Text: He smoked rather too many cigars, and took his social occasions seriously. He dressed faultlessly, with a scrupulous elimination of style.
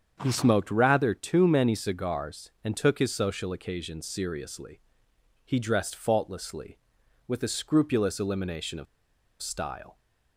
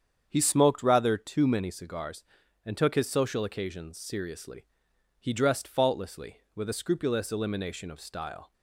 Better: second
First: starts louder than the rest; strong; until 1.2 s; 7.5 dB // pauses between "of" and "style"; noticeable; at 8.8 s; 0.55 s long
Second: starts louder than the rest; strong; until 1.3 s; 8 dB

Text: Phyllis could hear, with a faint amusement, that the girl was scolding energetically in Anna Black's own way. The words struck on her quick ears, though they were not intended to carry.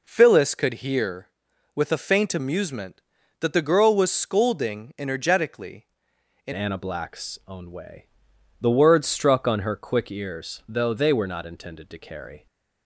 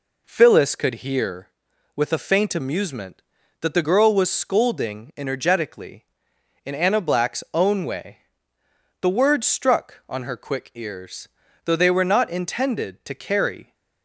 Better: second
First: changes voice at "Anna"; from 6.5 s on; 5.9 s long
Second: none

